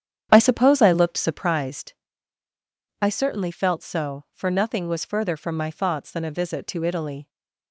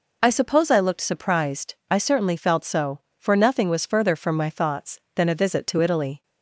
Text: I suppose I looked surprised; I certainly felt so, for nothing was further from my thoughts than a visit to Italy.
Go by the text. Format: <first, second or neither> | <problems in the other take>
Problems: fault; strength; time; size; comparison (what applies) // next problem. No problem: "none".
second | starts louder than the rest; strong; until 1.5 s; 9 dB